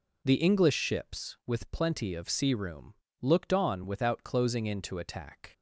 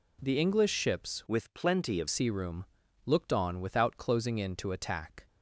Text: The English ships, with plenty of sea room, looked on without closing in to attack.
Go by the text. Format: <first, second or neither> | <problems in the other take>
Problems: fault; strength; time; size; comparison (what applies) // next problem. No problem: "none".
first | changes voice from "with" to "of"; from 1.2 to 2.0 s; 0.8 s long